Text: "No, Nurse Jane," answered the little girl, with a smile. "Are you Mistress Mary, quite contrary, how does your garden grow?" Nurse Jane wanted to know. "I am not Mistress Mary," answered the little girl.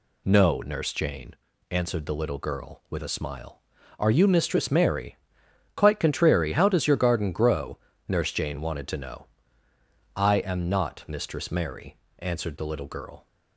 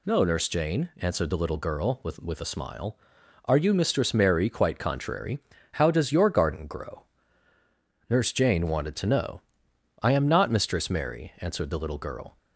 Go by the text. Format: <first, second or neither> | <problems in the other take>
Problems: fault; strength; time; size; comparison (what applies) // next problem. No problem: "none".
first | says "with" twice; at 2.1 s